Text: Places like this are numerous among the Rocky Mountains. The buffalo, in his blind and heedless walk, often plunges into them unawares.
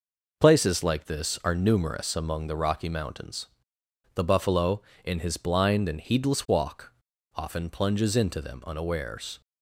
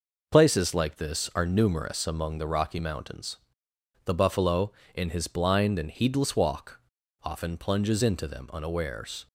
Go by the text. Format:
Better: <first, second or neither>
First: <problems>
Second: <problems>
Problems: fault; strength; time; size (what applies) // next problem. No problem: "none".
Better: neither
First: none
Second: none